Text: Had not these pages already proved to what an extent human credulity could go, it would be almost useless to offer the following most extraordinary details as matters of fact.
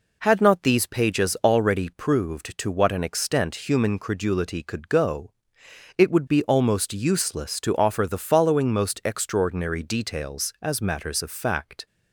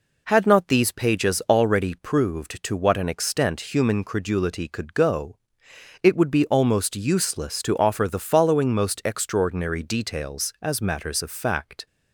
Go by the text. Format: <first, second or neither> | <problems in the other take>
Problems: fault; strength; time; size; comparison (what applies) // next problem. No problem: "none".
neither | none